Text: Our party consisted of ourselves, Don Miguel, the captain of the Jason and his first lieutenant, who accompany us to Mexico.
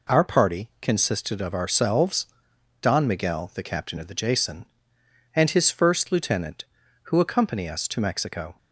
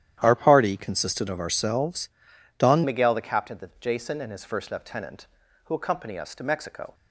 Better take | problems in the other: first | starts louder than the rest; strong; until 1.2 s; 11 dB // changes voice at "Miguel"; from 2.8 s on; 4.1 s long

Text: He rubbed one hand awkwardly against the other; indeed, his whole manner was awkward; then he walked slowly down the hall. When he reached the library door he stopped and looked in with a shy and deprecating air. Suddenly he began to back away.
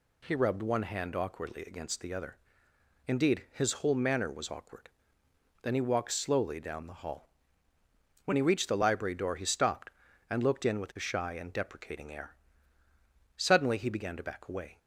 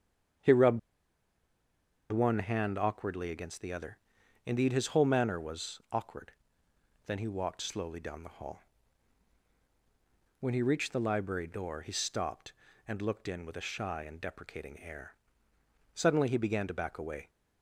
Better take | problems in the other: first | starts louder than the rest; strong; until 2.7 s; 7.5 dB // pauses between "rubbed" and "one"; strong; at 0.7 s; 1.3 s long

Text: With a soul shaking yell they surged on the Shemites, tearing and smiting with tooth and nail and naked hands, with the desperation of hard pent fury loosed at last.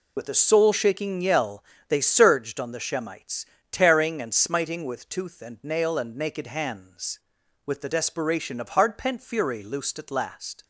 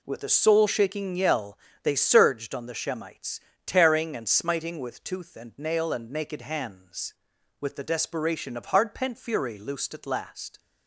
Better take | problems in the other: second | loses the start of "With"; at 0.1 s; 75 ms // pauses between "yell" and "they"; slight; at 1.6 s; 0.26 s long; slight in the second

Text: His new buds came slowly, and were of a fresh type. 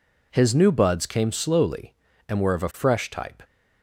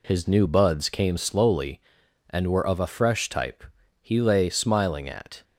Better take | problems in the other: first | goes on to say "He lay smiling at"; from 4.0 s on; 1.4 s long

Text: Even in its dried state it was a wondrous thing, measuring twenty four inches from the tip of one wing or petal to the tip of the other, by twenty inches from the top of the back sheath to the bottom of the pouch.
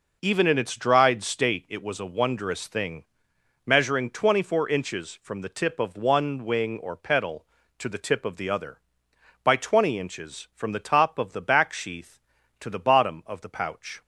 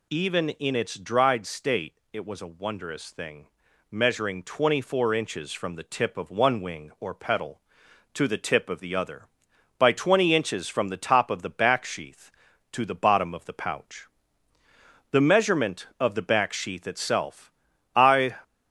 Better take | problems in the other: first | pauses between "state" and "it"; slight; at 1.9 s; 0.18 s long // goes on to say "The measurement of the back sheath itself I"; strong; from 15.1 s on; 3.2 s long

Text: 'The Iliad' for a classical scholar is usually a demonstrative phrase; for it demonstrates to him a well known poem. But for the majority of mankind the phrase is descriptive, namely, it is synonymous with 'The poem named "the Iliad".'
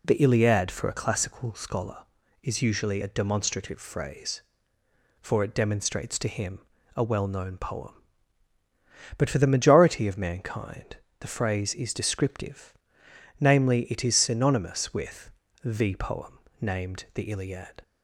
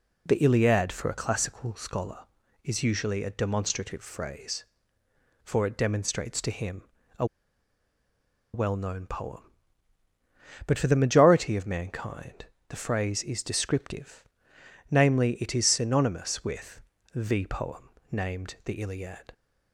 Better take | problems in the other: first | pauses between "him" and "a"; slight; at 6.8 s; 0.34 s long; slight in the first // pauses between "a" and "well"; strong; at 7.2 s; 1.2 s long // pauses between "mankind" and "the"; slight; at 12.4 s; 0.22 s long; slight in the first // pauses between "with" and "The"; slight; at 16.8 s; 0.32 s long; slight in the first // pauses between "poem" and "named"; slight; at 17.9 s; 0.20 s long; slight in the first

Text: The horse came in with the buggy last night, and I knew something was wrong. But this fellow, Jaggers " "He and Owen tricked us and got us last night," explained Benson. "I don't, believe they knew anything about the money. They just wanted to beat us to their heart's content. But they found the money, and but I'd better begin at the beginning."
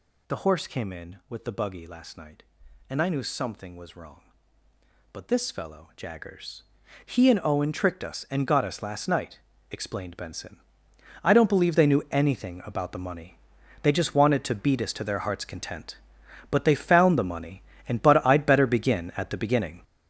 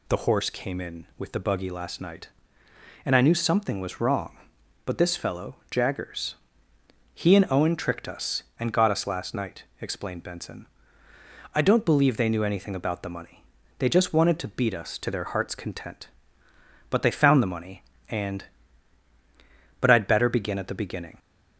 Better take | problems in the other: second | gets louder; strong; throughout; 8.5 dB

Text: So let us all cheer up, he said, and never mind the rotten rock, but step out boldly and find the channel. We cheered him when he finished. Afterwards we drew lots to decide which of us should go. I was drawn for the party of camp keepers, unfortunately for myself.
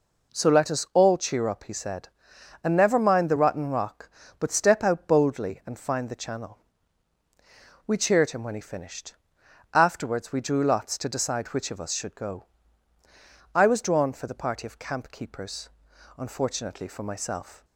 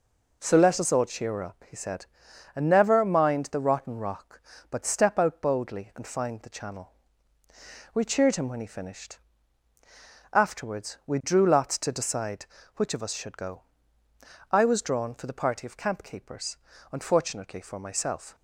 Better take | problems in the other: neither | none

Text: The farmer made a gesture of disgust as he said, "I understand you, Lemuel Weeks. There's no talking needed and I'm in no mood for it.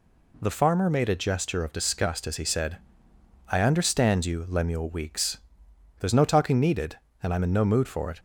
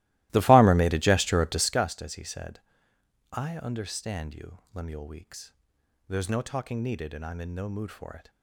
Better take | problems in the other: first | starts louder than the rest; strong; until 1.9 s; 17.5 dB

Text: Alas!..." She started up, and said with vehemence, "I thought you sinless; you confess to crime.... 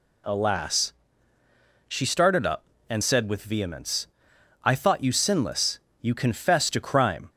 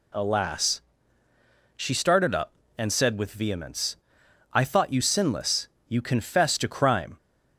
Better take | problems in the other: neither | none

